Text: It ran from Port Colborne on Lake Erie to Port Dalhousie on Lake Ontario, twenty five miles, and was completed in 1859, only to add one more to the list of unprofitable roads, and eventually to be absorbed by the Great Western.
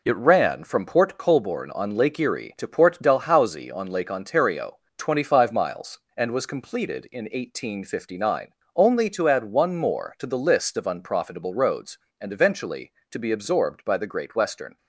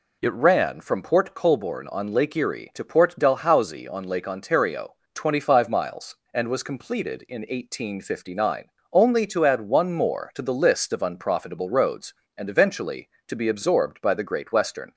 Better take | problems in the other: second | gets quieter; noticeable; throughout; 6 dB

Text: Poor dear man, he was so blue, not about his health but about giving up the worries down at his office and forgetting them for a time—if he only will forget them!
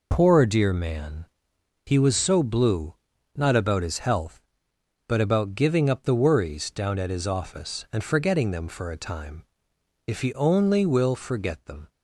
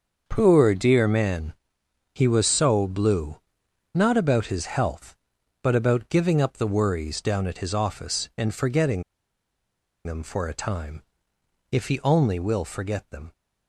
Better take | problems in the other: first | starts louder than the rest; until 1.2 s; 6.5 dB // pauses between "forgetting" and "them"; at 9.0 s; 1.0 s long

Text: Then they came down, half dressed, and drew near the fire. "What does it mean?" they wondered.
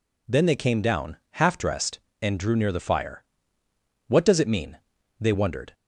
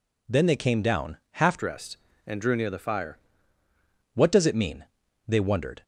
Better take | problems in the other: first | changes voice from "dressed" to "fire"; from 1.5 to 3.1 s; 1.6 s long

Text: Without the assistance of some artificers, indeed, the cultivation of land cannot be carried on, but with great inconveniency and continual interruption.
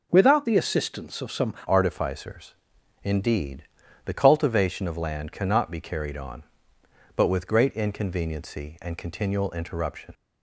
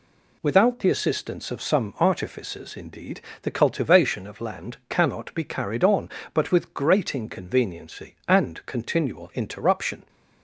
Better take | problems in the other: second | changes voice at "artificers"; from 1.6 s on; 8.5 s long

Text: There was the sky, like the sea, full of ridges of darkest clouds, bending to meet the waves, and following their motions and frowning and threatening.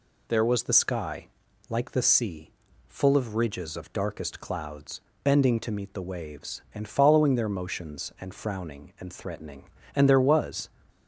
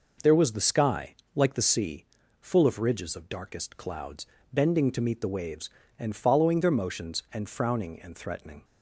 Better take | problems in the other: second | goes on to say "And there was"; noticeable; from 9.9 s on; 0.74 s long

